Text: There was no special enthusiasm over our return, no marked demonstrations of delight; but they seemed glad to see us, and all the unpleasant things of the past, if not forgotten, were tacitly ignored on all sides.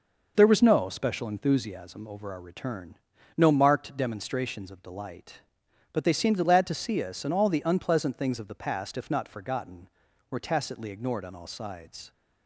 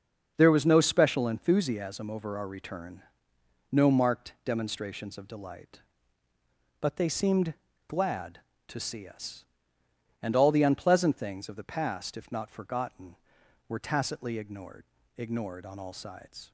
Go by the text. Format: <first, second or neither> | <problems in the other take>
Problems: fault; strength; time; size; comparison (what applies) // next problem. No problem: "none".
first | starts louder than the rest; until 1.3 s; 6.5 dB // pauses between "seemed" and "glad"; slight; at 7.5 s; 0.34 s long // says "ignored" twice; at 15.1 s